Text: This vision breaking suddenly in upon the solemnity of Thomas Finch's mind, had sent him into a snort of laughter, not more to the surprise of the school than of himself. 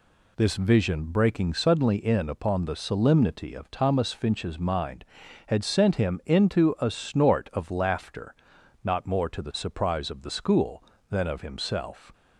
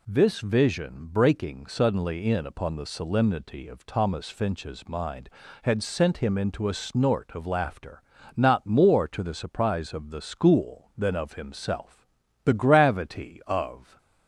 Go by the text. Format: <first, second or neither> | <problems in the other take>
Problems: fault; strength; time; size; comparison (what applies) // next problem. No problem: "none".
first | goes on to say "The gravity of"; from 12.4 s on; 1.5 s long